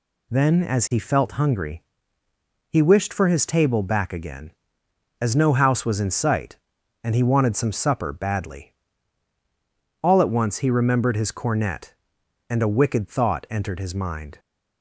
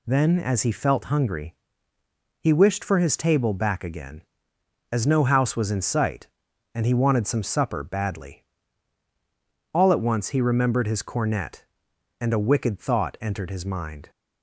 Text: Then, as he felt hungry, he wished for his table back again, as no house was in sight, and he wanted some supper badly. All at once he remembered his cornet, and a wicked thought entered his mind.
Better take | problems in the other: neither | none

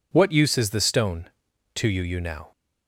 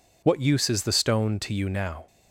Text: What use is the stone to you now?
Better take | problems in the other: second | says "you" twice; at 2.0 s

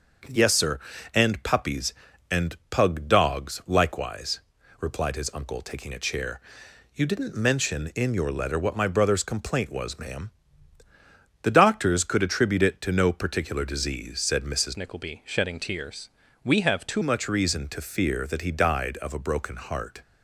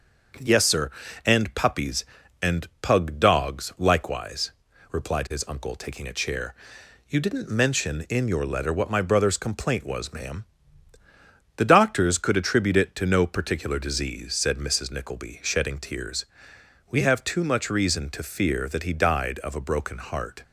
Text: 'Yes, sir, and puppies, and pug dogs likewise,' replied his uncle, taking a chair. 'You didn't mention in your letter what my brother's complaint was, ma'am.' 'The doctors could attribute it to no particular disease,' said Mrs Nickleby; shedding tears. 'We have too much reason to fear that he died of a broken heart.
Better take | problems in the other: second | starts louder than the rest; until 1.6 s; 6.5 dB; also in the second // changes voice from "Nickleby" to "too"; from 14.7 to 17.0 s; 2.3 s long

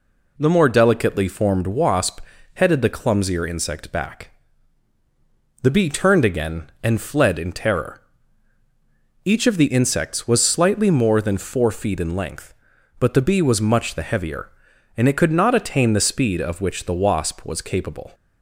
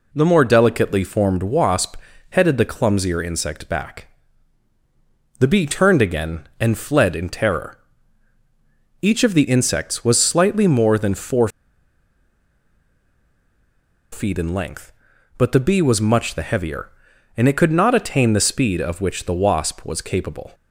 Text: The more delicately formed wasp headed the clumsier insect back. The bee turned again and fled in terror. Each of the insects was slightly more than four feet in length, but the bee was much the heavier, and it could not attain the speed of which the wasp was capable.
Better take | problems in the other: first | pauses between "wasp" and "headed"; slight; at 1.9 s; 0.34 s long; slight in the first // pauses between "four" and "feet"; strong; at 11.4 s; 2.6 s long

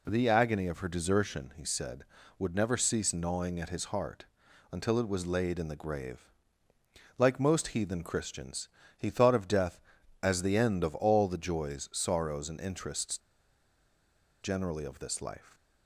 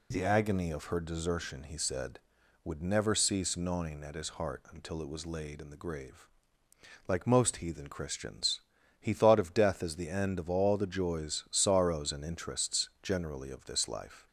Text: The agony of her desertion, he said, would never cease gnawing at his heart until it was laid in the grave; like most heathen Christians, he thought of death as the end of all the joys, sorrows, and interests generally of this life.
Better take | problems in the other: second | pauses between "heart" and "until"; at 4.2 s; 0.44 s long // pauses between "interests" and "generally"; at 13.1 s; 1.2 s long

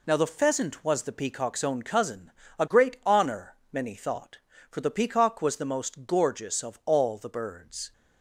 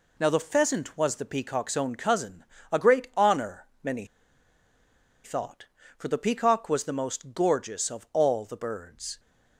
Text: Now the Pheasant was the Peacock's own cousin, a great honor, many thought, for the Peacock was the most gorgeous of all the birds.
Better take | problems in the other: first | pauses between "many" and "thought"; at 4.0 s; 1.1 s long

